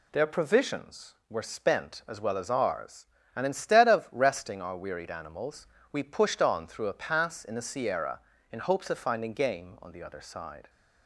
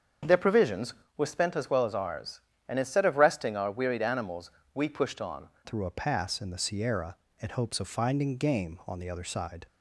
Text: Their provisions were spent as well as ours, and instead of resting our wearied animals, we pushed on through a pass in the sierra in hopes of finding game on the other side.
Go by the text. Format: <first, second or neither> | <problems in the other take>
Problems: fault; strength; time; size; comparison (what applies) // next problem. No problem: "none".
first | starts louder than the rest; strong; until 1.5 s; 7 dB // changes voice at "through"; from 5.6 s on; 4.0 s long